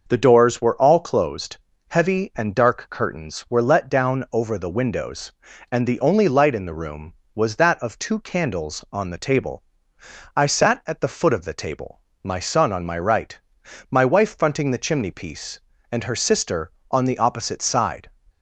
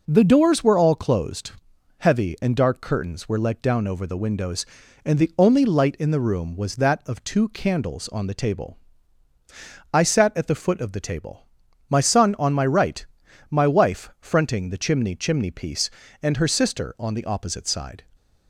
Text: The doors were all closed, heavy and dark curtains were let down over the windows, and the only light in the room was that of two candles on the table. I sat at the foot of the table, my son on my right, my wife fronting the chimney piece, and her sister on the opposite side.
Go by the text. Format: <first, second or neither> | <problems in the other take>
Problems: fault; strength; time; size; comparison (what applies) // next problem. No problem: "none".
first | says "chimney" twice; at 15.1 s